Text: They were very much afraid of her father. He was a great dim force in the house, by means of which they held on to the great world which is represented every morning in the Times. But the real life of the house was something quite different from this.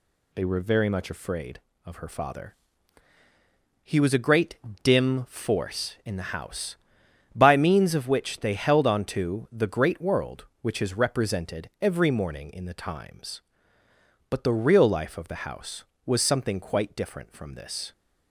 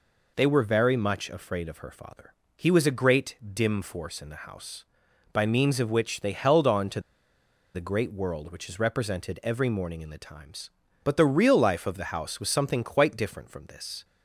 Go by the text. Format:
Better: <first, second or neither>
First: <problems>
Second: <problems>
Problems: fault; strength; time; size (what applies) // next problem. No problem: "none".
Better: first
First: pauses between "great" and "dim"; slight; at 4.5 s; 0.26 s long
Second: pauses between "great" and "dim"; slight; at 3.3 s; 0.18 s long // pauses between "to" and "the"; noticeable; at 6.9 s; 0.74 s long